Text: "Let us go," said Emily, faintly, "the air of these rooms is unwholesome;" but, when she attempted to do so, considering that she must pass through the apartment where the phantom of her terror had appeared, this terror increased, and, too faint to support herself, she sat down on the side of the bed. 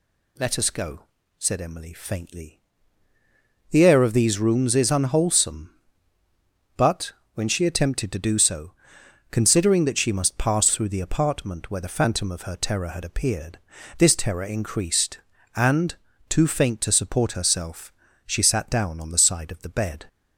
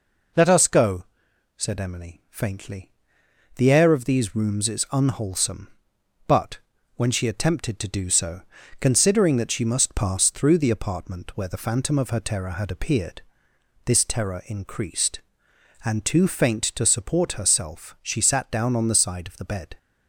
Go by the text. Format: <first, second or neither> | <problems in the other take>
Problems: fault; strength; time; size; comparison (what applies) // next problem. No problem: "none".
neither | none